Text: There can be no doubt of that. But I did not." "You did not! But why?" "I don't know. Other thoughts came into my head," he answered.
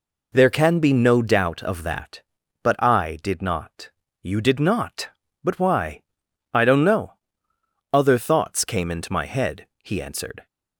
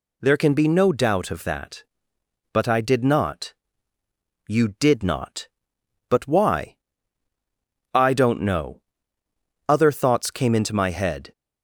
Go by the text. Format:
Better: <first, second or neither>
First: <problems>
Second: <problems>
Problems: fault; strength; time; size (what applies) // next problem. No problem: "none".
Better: first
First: none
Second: stops before "he answered"; at 11.3 s